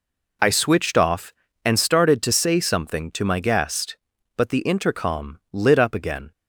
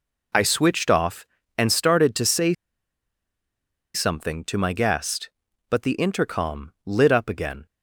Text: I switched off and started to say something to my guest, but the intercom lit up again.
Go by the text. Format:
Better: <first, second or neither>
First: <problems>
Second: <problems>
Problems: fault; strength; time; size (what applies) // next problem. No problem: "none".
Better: first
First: none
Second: pauses between "say" and "something"; strong; at 2.5 s; 1.4 s long